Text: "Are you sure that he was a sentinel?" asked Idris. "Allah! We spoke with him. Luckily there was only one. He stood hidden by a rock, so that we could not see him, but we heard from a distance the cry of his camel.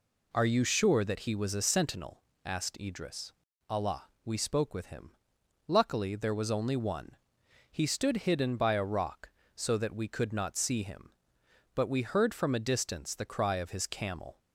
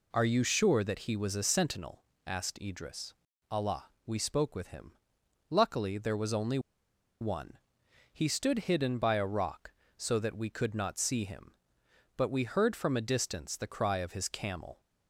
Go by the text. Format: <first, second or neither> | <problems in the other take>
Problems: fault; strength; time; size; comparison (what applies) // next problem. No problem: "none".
first | pauses between "only" and "one"; noticeable; at 6.5 s; 0.62 s long